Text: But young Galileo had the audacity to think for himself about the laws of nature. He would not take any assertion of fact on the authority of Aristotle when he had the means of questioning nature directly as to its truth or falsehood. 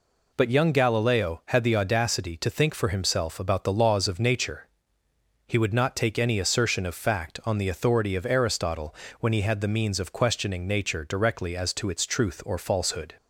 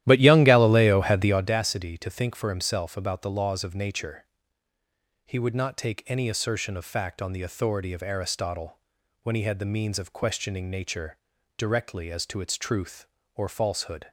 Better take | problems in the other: first | starts louder than the rest; strong; until 1.6 s; 13 dB // pauses between "Aristotle" and "when"; at 8.7 s; 0.44 s long; slight in the first // pauses between "nature" and "directly"; at 11.1 s; 0.40 s long

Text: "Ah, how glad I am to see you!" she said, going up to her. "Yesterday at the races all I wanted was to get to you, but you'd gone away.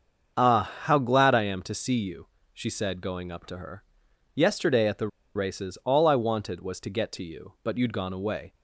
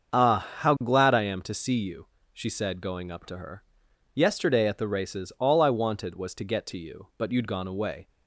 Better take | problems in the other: second | starts louder than the rest; until 1.4 s; 7 dB; also in the second // pauses between "the" and "races"; slight; at 5.0 s; 0.27 s long

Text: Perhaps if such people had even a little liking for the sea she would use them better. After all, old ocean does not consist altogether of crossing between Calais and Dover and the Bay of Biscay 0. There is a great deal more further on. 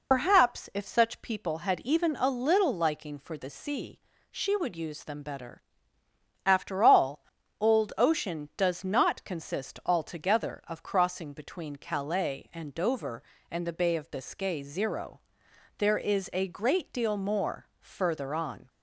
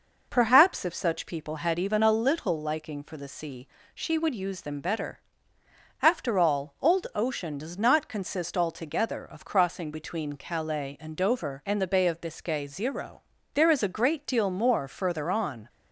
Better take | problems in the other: second | loses the start of "Perhaps"; at 0.1 s; 70 ms // pauses between "sea" and "she"; slight; at 3.9 s; 0.32 s long; slight in the second

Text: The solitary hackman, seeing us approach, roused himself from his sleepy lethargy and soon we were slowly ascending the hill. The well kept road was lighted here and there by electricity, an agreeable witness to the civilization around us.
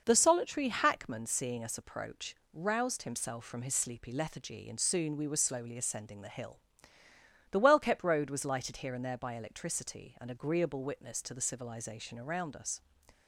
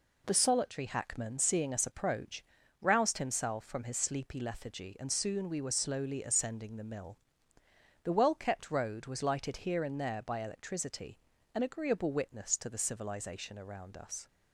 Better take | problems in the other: first | says "mill" for "hill"; at 6.8 s

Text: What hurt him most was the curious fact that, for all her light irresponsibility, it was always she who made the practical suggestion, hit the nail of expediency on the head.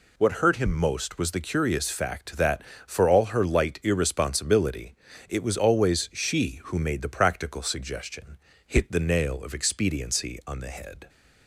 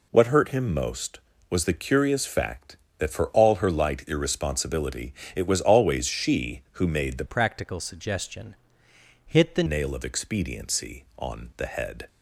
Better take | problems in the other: first | changes voice from "practical" to "the"; from 7.2 to 9.6 s; 2.4 s long

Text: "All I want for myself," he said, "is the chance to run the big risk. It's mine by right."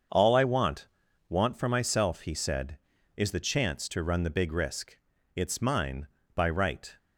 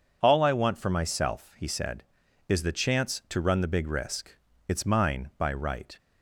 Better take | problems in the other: second | starts louder than the rest; until 1.5 s; 7 dB // says "want" twice; at 1.2 s

